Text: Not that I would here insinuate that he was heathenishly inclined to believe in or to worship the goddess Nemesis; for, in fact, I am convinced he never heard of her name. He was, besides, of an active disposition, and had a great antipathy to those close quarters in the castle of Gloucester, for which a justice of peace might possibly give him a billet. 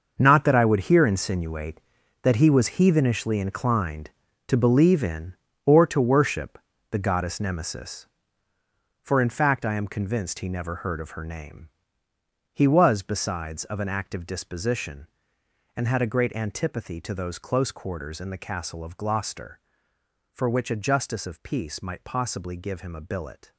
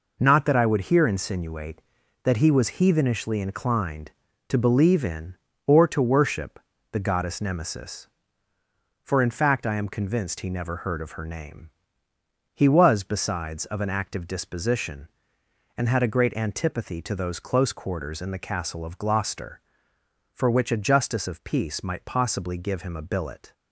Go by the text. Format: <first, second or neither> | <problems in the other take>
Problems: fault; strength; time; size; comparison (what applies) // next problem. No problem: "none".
second | gets quieter; strong; throughout; 12 dB // pauses between "worship" and "the"; slight; at 6.5 s; 0.32 s long; slight in the second